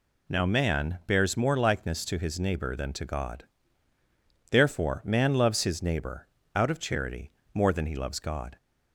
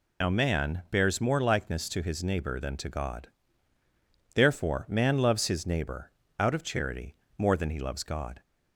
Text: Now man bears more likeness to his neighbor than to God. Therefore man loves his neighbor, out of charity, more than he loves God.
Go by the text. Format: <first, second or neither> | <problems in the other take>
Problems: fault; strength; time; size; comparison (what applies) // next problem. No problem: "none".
first | loses the start of "Now"; at 0.2 s; 75 ms